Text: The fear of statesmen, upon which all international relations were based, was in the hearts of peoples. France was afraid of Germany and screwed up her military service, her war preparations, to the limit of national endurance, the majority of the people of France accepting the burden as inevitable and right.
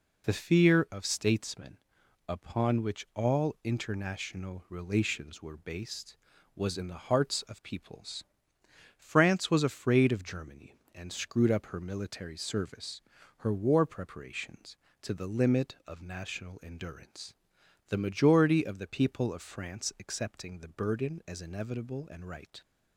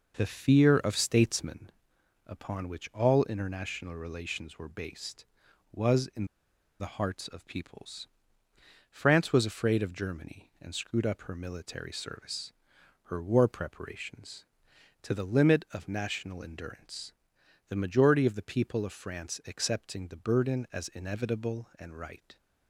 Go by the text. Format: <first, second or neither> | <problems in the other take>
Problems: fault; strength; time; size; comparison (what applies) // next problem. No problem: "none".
first | pauses between "in" and "the"; noticeable; at 6.2 s; 0.54 s long